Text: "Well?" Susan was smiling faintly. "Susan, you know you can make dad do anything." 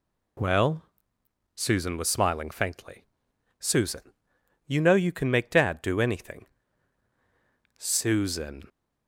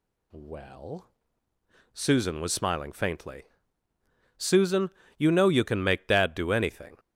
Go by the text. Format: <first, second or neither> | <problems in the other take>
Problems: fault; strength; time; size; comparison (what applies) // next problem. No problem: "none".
second | goes on to say "Susan"; noticeable; from 7.7 s on; 0.92 s long